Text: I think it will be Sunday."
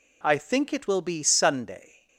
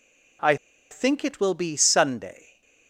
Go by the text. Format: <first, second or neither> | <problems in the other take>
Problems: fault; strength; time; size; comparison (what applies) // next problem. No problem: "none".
first | pauses between "I" and "think"; slight; at 0.5 s; 0.34 s long